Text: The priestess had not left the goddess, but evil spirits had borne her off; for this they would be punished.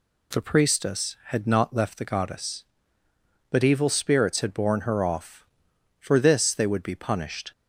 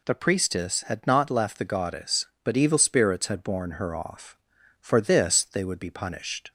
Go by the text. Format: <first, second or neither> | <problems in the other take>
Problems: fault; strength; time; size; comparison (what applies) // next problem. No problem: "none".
neither | none